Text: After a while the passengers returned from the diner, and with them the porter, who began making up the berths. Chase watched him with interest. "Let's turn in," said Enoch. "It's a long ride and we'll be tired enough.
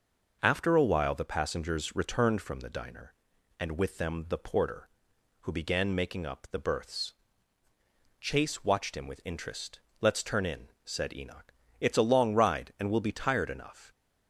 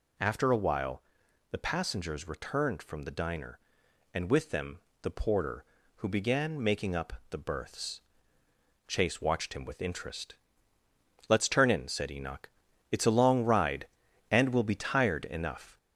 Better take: first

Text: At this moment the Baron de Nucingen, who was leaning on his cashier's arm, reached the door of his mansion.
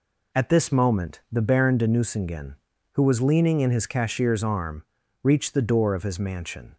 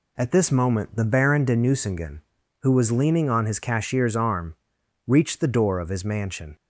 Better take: second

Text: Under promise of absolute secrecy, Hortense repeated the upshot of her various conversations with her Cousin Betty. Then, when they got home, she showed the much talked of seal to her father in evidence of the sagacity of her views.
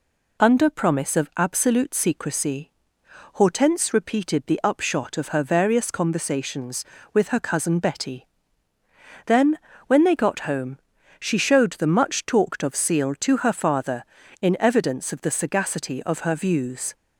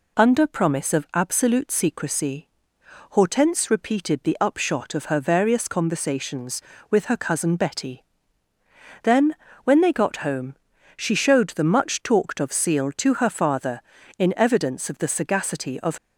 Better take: first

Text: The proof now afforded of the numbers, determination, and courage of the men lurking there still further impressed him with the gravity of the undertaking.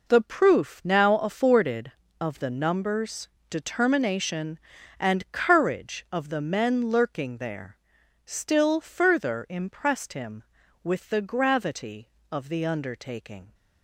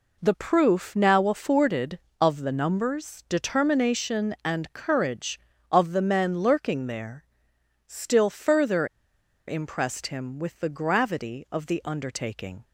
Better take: first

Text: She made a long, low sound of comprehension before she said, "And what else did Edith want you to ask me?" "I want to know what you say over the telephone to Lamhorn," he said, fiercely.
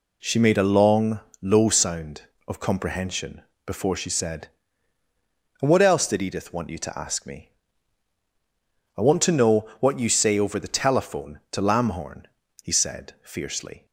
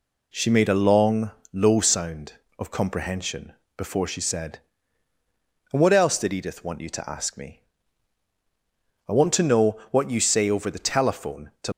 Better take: first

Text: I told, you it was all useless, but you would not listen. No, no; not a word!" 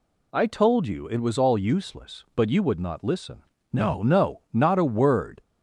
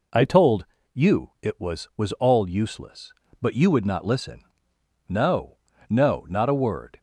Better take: first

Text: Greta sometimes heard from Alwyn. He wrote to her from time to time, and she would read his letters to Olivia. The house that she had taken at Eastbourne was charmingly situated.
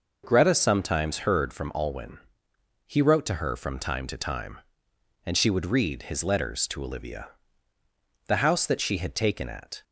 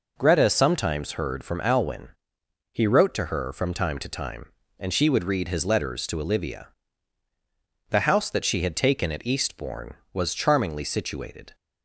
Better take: second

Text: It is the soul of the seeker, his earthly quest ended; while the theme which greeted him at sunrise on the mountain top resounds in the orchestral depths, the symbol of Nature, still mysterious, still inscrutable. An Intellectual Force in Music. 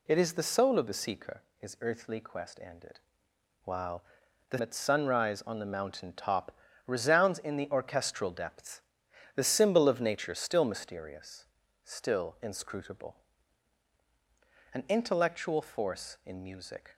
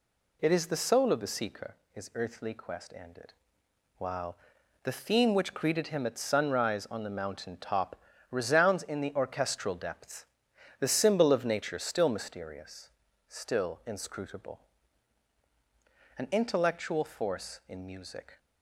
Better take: second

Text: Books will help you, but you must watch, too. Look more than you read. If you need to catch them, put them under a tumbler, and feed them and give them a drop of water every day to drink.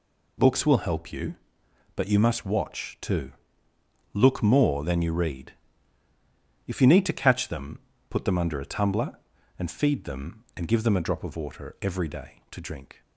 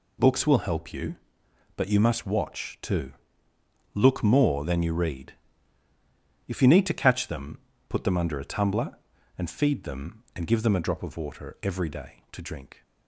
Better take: neither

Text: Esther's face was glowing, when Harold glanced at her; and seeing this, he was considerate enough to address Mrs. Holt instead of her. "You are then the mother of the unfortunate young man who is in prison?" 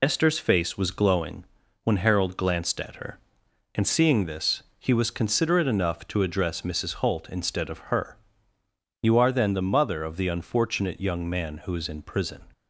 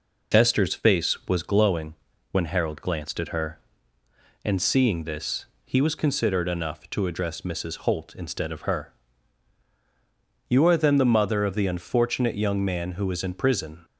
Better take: second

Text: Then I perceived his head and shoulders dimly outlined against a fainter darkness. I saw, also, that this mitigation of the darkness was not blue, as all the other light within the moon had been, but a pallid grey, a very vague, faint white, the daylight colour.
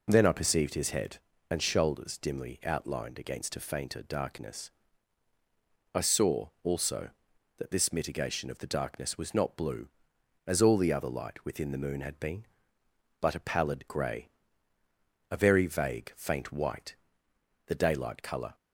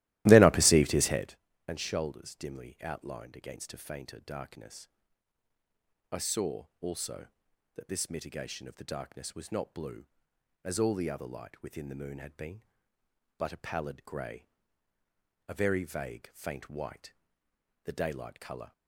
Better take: first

